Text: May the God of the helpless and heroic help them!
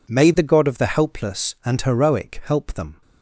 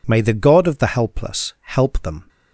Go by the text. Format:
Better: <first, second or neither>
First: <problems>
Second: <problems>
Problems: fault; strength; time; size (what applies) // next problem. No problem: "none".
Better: first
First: none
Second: skips "and heroic"; at 1.5 s